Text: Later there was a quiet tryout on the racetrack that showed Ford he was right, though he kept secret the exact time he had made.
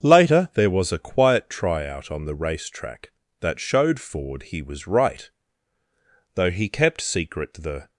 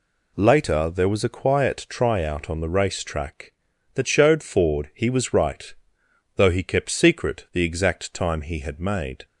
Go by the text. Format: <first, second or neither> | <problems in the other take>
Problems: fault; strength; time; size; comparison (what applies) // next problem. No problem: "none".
second | starts louder than the rest; until 1.0 s; 7 dB // stops before "exact time he had made"; at 7.9 s